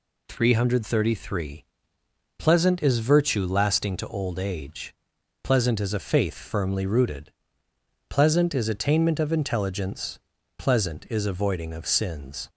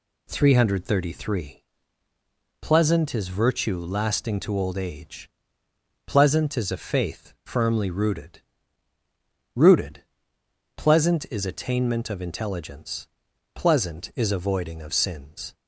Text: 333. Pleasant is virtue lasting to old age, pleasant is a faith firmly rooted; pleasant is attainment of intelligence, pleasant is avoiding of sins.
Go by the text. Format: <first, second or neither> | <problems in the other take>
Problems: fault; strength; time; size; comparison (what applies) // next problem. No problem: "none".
first | says "rooted" twice; at 9.5 s